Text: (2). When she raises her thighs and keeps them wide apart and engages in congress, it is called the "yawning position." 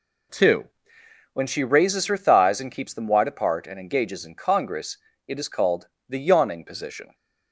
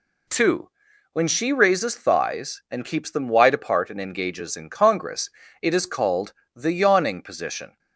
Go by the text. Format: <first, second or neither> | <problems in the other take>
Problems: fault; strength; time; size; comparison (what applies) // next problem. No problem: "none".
first | skips "her"; at 1.9 s // pauses between "called" and "the"; slight; at 6.3 s; 0.20 s long; slight in the first